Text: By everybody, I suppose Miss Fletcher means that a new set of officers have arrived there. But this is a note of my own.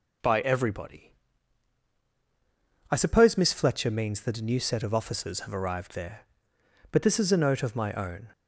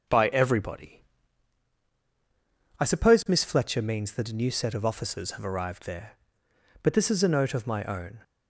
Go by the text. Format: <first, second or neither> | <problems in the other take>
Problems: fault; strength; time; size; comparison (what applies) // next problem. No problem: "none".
first | starts louder than the rest; noticeable; until 1.5 s; 6 dB